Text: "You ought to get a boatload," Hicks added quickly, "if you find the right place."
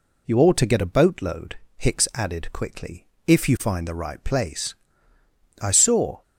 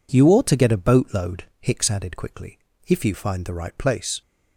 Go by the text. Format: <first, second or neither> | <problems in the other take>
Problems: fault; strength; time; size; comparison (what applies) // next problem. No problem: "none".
second | goes on to say "I saw"; from 5.6 s on; 0.60 s long